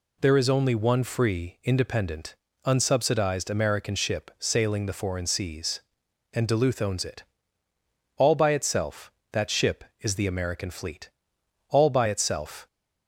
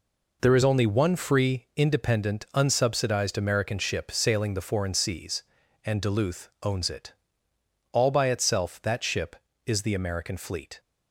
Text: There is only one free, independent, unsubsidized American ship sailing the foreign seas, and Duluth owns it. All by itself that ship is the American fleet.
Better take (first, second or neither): second